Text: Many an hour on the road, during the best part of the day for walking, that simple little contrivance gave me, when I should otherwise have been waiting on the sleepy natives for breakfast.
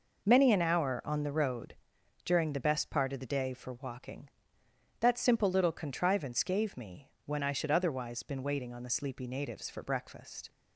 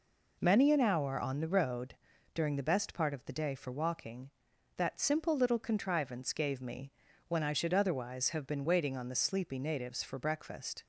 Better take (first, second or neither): second